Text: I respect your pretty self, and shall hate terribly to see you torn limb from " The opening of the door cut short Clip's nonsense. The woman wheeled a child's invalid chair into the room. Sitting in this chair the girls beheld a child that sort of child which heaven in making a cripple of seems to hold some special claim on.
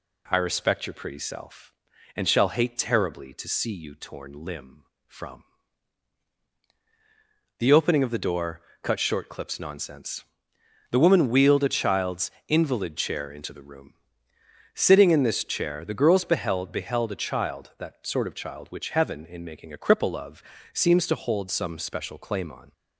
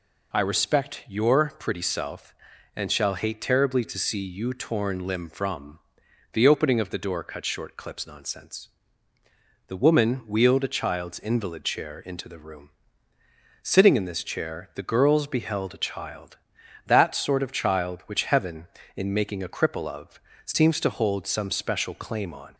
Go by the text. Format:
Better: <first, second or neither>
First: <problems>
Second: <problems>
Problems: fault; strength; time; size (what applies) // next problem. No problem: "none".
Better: second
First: pauses between "door" and "cut"; slight; at 8.6 s; 0.22 s long // pauses between "child's" and "invalid"; slight; at 12.3 s; 0.16 s long // says "beheld" twice; at 16.7 s // pauses between "of" and "seems"; slight; at 20.4 s; 0.30 s long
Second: pauses between "of" and "seems"; slight; at 20.2 s; 0.24 s long